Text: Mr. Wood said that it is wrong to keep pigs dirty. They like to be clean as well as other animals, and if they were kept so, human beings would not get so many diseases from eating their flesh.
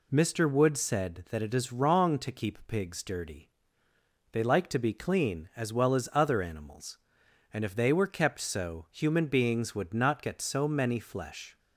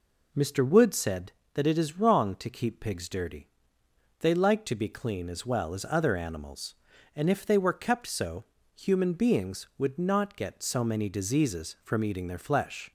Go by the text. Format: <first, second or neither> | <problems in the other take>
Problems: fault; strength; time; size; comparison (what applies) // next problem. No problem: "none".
second | skips "diseases from eating their"; at 10.9 s